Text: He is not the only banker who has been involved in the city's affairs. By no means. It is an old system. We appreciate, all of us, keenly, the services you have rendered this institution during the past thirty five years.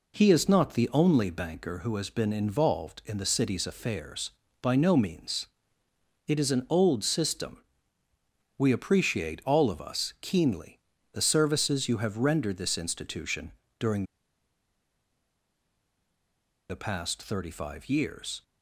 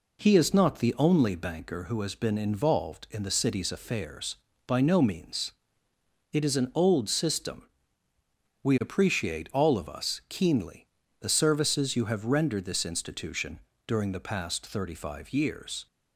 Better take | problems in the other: second | pauses between "institution" and "during"; slight; at 13.5 s; 0.26 s long; slight in the second // pauses between "during" and "the"; strong; at 14.0 s; 2.6 s long

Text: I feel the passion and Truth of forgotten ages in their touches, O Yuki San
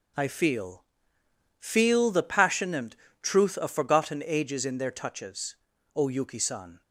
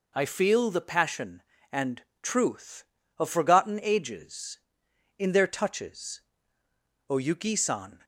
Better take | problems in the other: second | says "feel" twice; at 1.5 s // pauses between "and" and "Truth"; slight; at 2.9 s; 0.26 s long; slight in the second

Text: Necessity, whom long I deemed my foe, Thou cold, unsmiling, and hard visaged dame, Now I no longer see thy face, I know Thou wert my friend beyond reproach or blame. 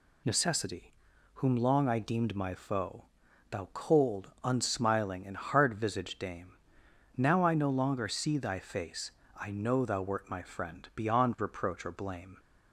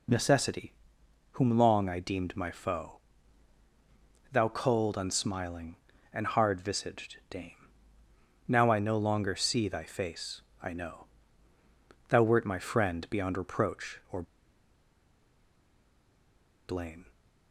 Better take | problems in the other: first | pauses between "know" and "Thou"; at 11.0 s; 1.0 s long // pauses between "or" and "blame"; strong; at 14.2 s; 2.4 s long

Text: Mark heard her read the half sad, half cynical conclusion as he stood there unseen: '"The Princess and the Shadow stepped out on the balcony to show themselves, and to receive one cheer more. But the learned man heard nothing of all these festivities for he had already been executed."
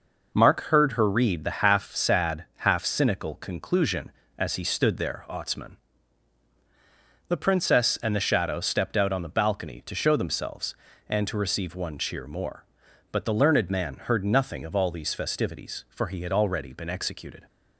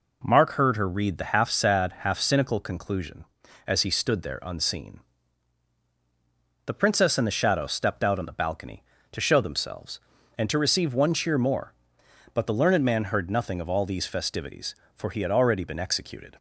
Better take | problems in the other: second | says "otsman" for "unseen"; at 5.2 s

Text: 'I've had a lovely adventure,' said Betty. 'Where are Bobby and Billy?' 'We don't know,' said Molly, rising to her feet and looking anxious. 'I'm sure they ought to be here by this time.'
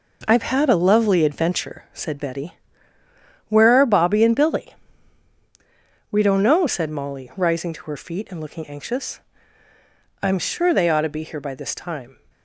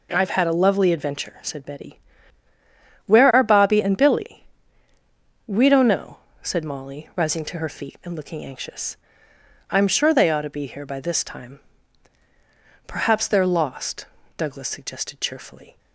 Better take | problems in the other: first | goes on to say "Perhaps they're lost Douglas suggested cheerfully"; strong; from 12.8 s on; 2.9 s long

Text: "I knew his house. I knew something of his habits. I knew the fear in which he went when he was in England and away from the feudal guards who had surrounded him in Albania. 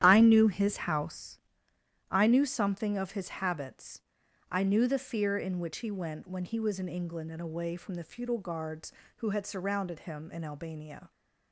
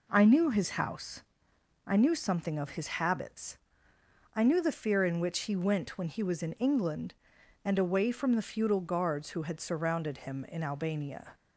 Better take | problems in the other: second | starts louder than the rest; strong; until 1.3 s; 11 dB

